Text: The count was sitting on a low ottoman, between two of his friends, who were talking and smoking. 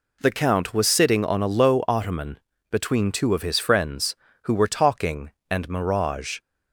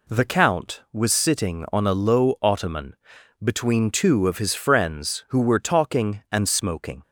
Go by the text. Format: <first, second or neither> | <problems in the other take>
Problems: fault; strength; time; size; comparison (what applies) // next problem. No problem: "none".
second | says "mirage" for "smoking"; at 5.6 s